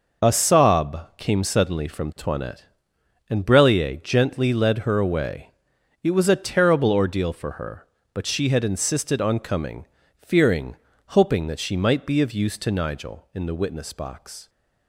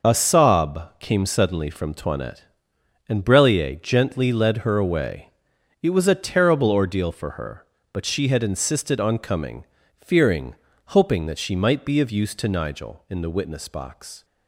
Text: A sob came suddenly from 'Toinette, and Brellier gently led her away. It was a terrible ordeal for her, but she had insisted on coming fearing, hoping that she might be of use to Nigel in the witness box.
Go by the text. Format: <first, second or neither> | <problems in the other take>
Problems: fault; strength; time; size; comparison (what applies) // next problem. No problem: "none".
neither | pauses between "coming" and "fearing"; slight; the same in both